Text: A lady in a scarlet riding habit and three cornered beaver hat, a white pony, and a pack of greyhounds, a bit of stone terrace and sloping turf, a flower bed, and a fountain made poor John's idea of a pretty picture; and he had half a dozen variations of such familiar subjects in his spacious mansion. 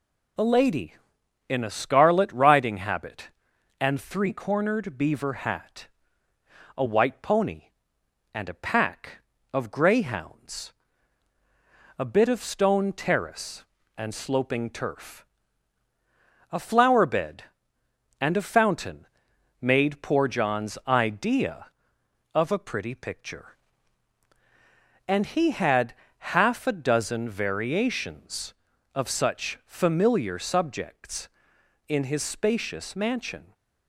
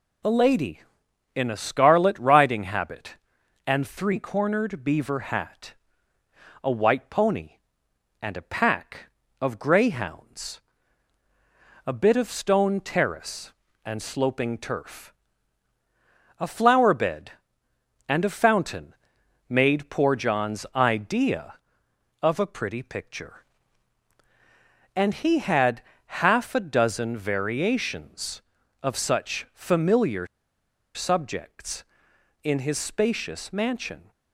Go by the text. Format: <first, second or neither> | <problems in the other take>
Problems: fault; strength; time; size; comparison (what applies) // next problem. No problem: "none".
first | pauses between "fountain" and "made"; noticeable; at 18.9 s; 0.54 s long; noticeable in the first // pauses between "had" and "half"; slight; at 25.8 s; 0.26 s long; slight in the first // pauses between "familiar" and "subjects"; noticeable; at 30.2 s; 0.70 s long